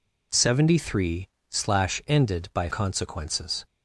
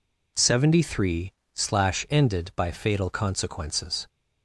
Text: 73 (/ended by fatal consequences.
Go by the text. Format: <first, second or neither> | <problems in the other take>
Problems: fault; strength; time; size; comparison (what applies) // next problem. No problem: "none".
second | skips "fatal"; at 2.6 s